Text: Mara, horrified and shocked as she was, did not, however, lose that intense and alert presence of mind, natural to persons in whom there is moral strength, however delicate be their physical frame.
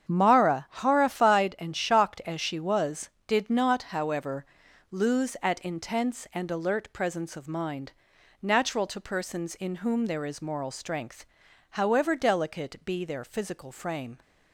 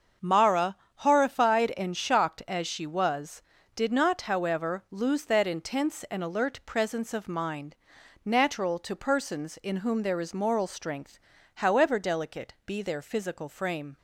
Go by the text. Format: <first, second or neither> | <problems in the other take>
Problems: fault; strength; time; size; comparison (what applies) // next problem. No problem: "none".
second | starts louder than the rest; strong; until 1.1 s; 8 dB; also in the second // says "at" for "that"; at 5.4 s